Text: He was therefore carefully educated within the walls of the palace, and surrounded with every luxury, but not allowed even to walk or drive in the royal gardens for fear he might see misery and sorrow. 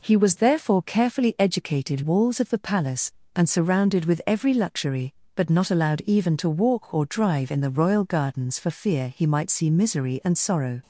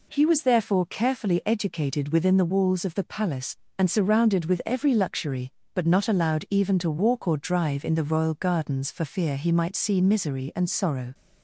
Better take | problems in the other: second | skips "within the"; at 2.0 s

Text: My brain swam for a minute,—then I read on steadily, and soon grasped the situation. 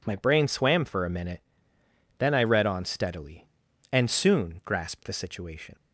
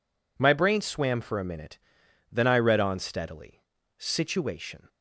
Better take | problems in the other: first | skips "and soon grasped the"; at 3.7 s

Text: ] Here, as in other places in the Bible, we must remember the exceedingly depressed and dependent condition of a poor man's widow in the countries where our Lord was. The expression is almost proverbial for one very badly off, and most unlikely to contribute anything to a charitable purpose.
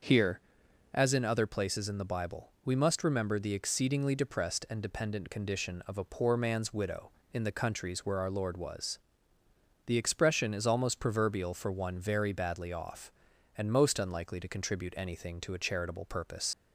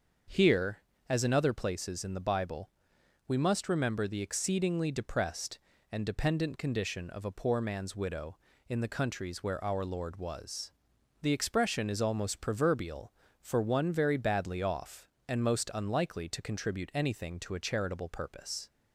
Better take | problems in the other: second | starts louder than the rest; noticeable; until 1.5 s; 6 dB; also in the second // leaves "purpose" unfinished; at 16.5 s; 60 ms

